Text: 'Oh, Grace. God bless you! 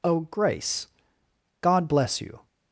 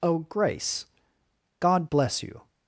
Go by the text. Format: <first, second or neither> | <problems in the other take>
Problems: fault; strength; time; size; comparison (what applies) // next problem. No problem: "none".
neither | none